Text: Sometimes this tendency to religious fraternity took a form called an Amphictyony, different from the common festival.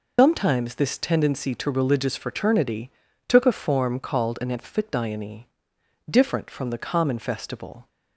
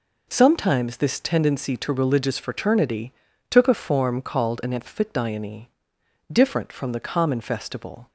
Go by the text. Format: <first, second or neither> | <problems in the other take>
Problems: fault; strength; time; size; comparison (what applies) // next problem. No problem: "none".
second | loses the start of "Sometimes"; at 0.1 s; 120 ms // pauses between "fraternity" and "took"; slight; at 2.9 s; 0.36 s long; slight in the second